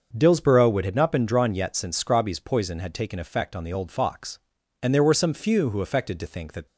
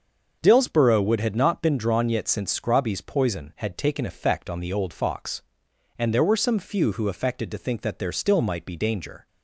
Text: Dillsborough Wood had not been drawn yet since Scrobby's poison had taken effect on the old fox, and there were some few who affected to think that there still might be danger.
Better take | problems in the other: second | starts louder than the rest; until 1.1 s; 6.5 dB; also in the second // stops before "there still might be danger"; at 6.6 s

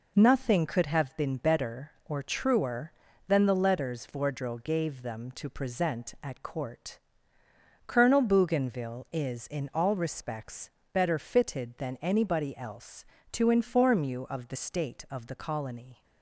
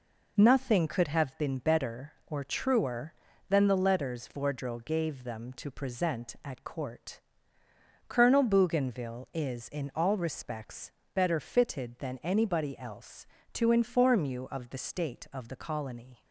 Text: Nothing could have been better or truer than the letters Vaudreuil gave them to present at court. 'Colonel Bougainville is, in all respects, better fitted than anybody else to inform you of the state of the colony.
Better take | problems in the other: neither | none

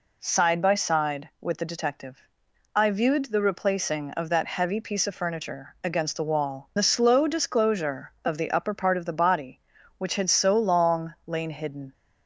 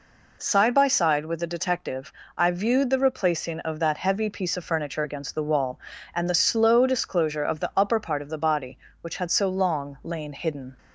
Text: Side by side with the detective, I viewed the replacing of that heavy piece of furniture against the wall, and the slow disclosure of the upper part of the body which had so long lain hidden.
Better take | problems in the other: second | skips "and"; at 6.7 s

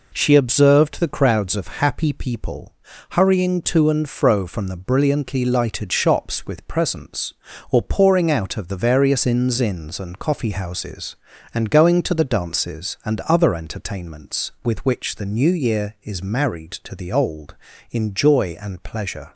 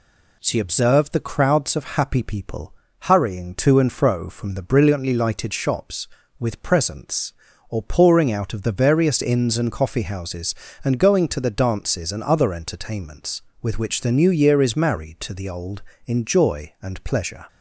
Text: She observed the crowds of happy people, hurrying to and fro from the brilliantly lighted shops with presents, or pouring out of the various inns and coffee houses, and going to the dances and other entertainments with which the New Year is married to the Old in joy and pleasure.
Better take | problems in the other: second | says "inns" twice; at 9.5 s

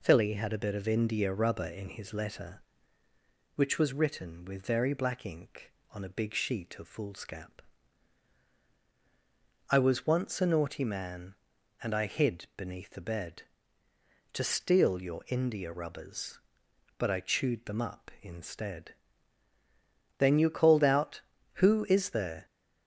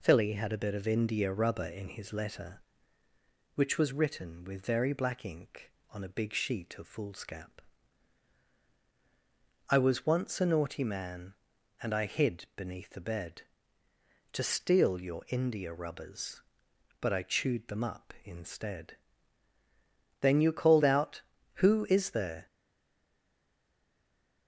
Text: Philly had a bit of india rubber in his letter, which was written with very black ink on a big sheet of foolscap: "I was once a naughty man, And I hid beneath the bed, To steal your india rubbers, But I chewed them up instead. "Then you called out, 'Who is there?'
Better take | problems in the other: first | stays silent after the last word; noticeable; from 22.4 s on; 2.0 s long

